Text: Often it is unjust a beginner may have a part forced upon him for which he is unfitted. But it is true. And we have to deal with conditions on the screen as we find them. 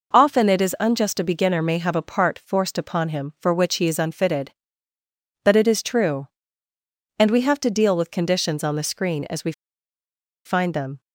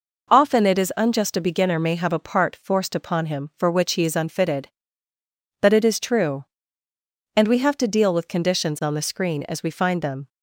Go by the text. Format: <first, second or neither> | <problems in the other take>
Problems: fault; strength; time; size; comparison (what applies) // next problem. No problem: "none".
second | pauses between "we" and "find"; noticeable; at 9.5 s; 0.93 s long